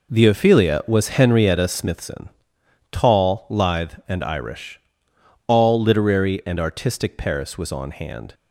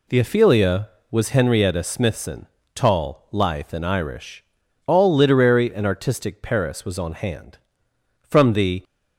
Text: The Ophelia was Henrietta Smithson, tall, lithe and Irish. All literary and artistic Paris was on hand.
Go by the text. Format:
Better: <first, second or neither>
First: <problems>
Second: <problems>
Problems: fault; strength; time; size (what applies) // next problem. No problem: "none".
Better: first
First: none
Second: goes on to say "From the"; noticeable; from 8.2 s on; 0.62 s long